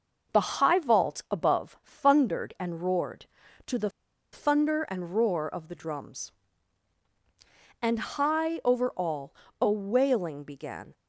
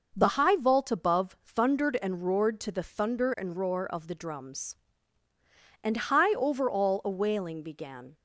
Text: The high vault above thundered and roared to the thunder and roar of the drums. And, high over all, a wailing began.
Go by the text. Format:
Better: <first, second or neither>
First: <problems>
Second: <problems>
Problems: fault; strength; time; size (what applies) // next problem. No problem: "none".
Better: second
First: pauses between "the" and "thunder"; at 3.8 s; 0.43 s long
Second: none